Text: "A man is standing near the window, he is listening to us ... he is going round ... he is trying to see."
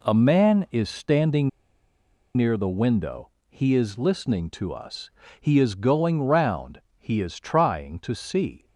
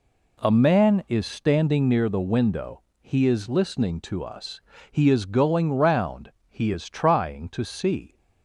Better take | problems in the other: second | pauses between "standing" and "near"; noticeable; at 1.4 s; 0.86 s long

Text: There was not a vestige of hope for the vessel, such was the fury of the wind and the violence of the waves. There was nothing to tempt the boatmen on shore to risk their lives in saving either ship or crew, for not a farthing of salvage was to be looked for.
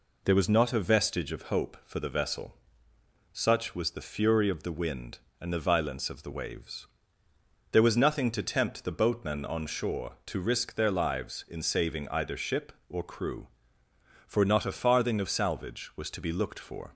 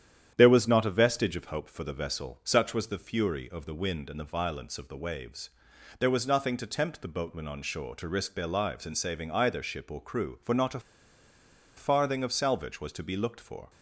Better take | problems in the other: first | starts louder than the rest; strong; until 1.3 s; 9.5 dB // pauses between "a" and "farthing"; noticeable; at 10.7 s; 0.97 s long

